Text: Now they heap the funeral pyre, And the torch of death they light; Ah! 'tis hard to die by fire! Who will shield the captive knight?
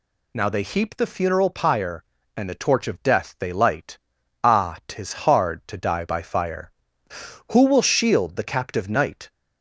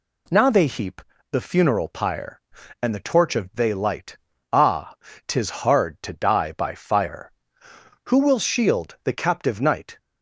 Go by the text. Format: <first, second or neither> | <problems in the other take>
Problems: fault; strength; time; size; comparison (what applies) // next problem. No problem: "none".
first | pauses between "heap" and "the"; slight; at 1.0 s; 0.28 s long // skips "death"; at 3.5 s